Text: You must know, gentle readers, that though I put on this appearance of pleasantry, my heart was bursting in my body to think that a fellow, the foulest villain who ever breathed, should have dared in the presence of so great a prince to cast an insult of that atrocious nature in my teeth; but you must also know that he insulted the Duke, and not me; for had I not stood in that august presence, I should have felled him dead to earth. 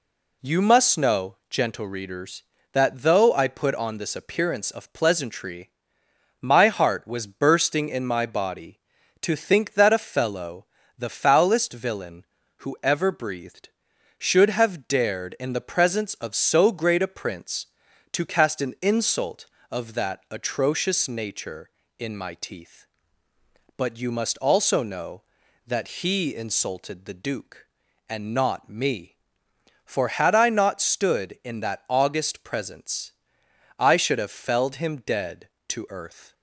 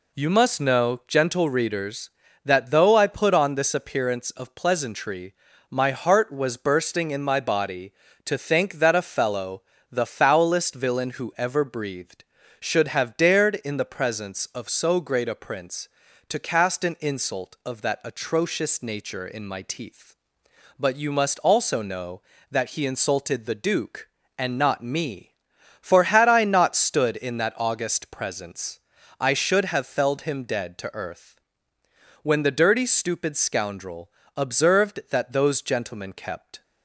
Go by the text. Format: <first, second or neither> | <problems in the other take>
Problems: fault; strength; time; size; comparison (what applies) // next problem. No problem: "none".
first | goes on to say "When the dirty stupid scoundrel observed that those gentlemen kept"; strong; from 32.2 s on; 4.4 s long